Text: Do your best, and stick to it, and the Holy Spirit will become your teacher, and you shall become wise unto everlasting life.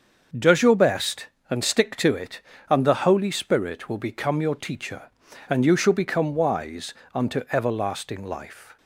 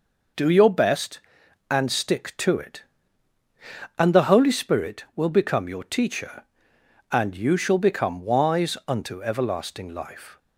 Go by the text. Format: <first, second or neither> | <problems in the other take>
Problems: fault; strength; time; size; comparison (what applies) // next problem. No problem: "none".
second | starts louder than the rest; until 1.5 s; 6.5 dB // says "Does" for "Do"; at 0.3 s // pauses between "wise" and "unto"; slight; at 6.9 s; 0.20 s long